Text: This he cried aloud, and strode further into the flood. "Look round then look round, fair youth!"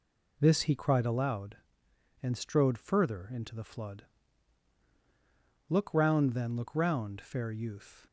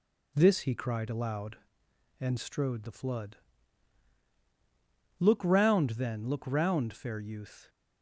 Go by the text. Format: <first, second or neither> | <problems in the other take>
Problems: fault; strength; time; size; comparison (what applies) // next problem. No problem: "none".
first | skips "further into"; at 2.8 s